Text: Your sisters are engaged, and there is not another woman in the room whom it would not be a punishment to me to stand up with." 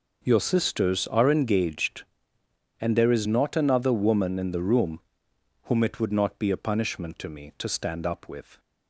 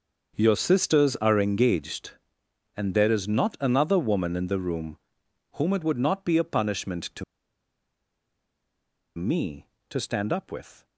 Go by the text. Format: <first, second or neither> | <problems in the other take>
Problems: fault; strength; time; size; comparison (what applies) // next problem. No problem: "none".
first | starts louder than the rest; until 1.4 s; 6.5 dB // pauses between "room" and "whom"; noticeable; at 4.9 s; 0.56 s long; noticeable in the first // pauses between "to" and "me"; strong; at 7.2 s; 1.9 s long